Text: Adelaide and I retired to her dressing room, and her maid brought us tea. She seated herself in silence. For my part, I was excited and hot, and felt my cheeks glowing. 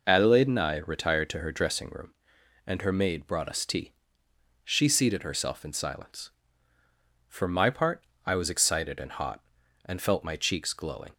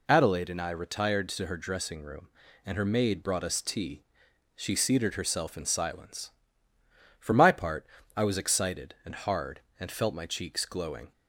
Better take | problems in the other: first | says "hard" for "hot"; at 9.1 s

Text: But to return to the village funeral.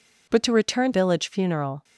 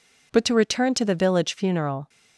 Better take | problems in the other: second | skips "to the"; at 0.9 s

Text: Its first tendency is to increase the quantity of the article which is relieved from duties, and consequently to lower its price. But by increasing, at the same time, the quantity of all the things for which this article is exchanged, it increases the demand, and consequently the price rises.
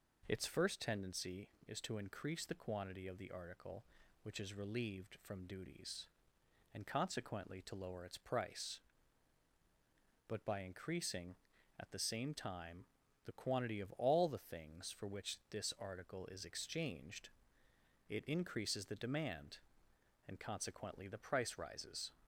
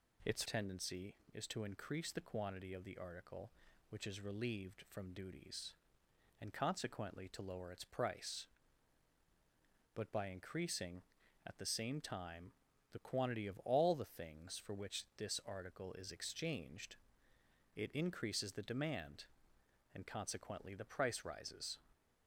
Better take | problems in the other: first | skips "first"; at 0.4 s

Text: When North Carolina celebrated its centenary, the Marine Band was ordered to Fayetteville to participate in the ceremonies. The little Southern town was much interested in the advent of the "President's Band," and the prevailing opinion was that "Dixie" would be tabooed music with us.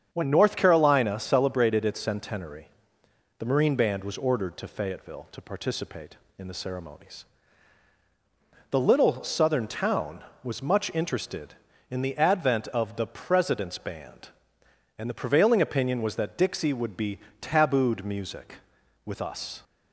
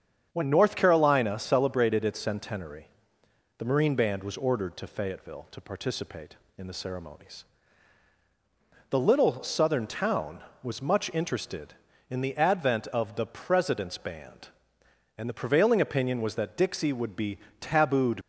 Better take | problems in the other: first | starts louder than the rest; strong; until 1.3 s; 8 dB; strong in the first // pauses between "be" and "tabooed"; slight; at 17.3 s; 0.20 s long; slight in the first // stops before "music with us"; at 18.2 s

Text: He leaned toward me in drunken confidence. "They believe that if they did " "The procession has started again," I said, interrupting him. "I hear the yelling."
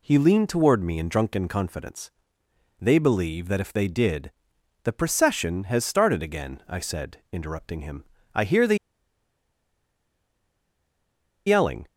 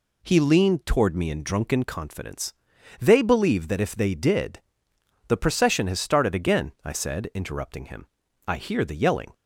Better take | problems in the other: second | pauses between "the" and "yelling"; strong; at 8.7 s; 2.7 s long

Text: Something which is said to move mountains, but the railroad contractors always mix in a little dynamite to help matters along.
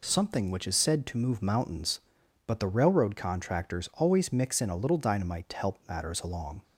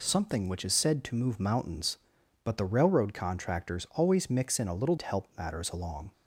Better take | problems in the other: first | skips "dynamite"; at 4.9 s

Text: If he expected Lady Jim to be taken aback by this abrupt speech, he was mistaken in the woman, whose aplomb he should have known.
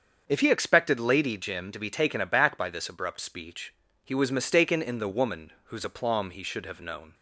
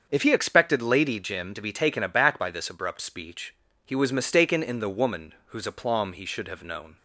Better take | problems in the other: neither | starts louder than the rest; the same in both

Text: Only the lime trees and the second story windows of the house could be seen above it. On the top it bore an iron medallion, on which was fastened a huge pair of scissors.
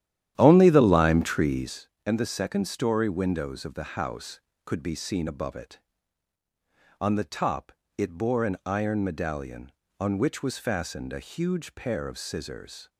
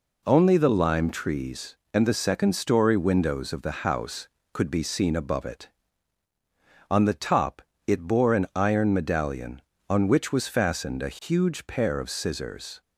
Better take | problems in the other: second | starts louder than the rest; strong; until 1.8 s; 11.5 dB // pauses between "top" and "it"; slight; at 7.7 s; 0.26 s long; slight in the second

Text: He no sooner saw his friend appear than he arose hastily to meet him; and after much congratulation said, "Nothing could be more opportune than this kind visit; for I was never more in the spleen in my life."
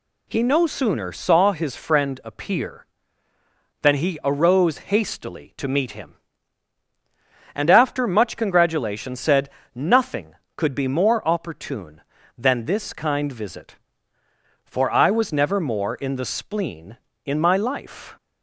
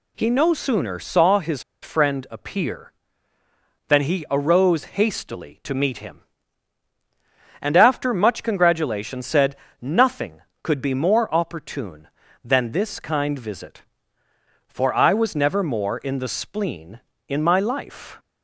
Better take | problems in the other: first | pauses between "his" and "friend"; slight; at 1.6 s; 0.20 s long // pauses between "arose" and "hastily"; slight; at 4.8 s; 0.16 s long; slight in the first

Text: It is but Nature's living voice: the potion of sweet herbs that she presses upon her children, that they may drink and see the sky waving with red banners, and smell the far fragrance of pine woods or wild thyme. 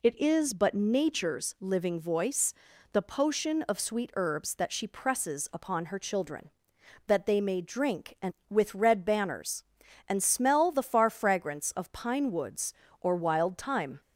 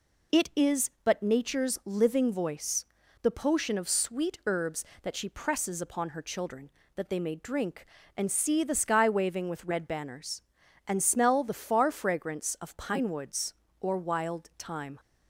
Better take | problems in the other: second | skips "see the sky waving"; at 8.4 s

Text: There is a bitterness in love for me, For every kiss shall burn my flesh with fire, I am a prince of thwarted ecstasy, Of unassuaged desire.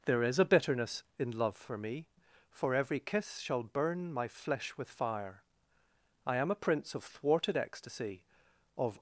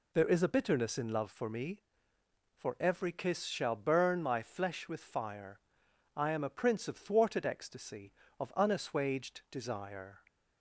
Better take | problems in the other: second | stops before "unassuaged desire"; at 8.9 s

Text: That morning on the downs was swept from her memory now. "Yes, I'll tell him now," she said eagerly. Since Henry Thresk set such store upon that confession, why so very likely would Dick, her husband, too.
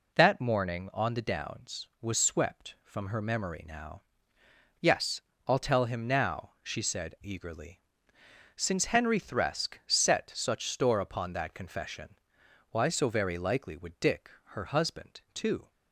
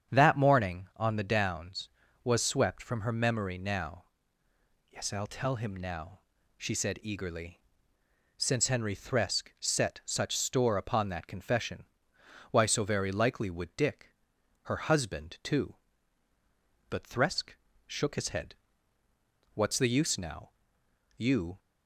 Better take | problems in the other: first | starts louder than the rest; strong; until 1.1 s; 8 dB // goes on to say "But Thresk shook his head What's the use now You"; strong; from 16.8 s on; 4.7 s long

